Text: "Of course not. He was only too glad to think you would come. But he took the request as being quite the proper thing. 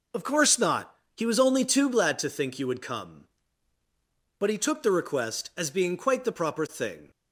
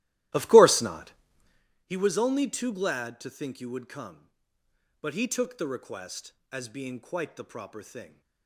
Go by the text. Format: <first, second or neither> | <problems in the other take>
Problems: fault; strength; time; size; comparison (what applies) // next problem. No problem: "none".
first | starts louder than the rest; strong; until 1.6 s; 15.5 dB